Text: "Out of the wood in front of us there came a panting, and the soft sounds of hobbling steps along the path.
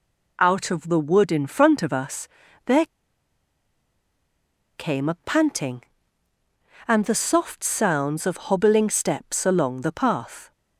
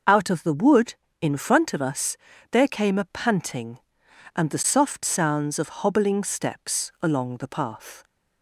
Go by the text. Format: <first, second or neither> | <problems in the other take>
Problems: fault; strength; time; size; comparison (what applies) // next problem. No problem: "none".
second | pauses between "us" and "there"; at 2.2 s; 0.38 s long; slight in the second // pauses between "there" and "came"; strong; at 2.8 s; 1.9 s long